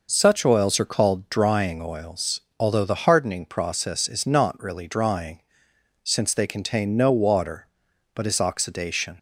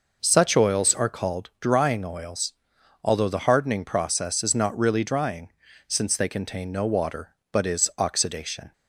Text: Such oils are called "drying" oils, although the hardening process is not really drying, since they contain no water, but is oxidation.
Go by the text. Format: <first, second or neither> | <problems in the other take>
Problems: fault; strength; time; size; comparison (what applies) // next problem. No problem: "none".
neither | none